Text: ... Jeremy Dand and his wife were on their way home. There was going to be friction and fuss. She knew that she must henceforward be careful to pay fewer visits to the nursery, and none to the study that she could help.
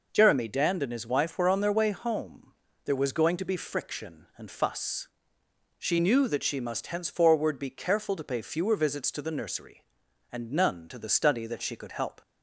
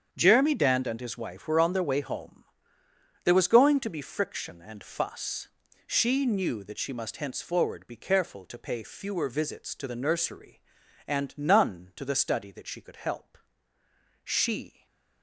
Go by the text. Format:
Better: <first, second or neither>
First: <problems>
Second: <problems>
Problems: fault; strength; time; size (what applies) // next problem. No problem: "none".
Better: first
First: none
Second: starts louder than the rest; strong; until 1.1 s; 7.5 dB // goes on to say "She"; noticeable; from 14.2 s on; 0.62 s long // stays silent after the last word; slight; from 14.6 s on; 0.6 s long